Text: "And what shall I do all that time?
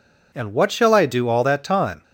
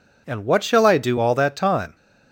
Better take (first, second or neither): neither